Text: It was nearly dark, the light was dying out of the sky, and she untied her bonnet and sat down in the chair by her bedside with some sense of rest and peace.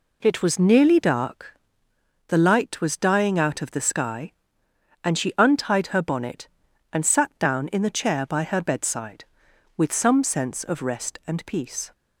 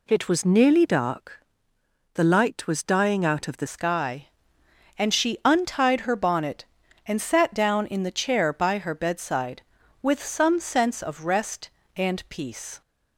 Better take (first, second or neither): first